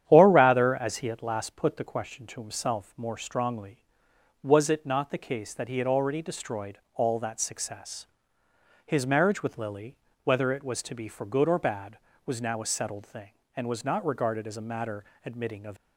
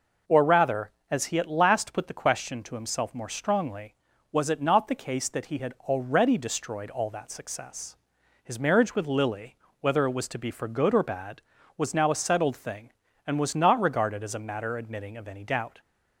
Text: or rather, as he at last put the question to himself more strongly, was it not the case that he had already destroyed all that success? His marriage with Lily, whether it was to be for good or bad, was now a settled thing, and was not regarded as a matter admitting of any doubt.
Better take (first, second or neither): second